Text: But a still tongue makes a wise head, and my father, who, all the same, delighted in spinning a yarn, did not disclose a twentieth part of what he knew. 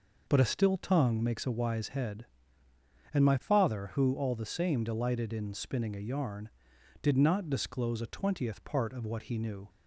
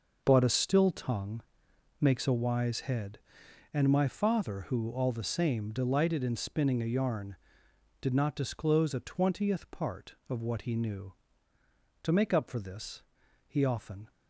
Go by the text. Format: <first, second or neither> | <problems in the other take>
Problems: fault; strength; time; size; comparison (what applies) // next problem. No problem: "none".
first | pauses between "tongue" and "makes"; noticeable; at 1.4 s; 0.56 s long // goes on to say "To make up for this he often"; strong; from 12.0 s on; 2.0 s long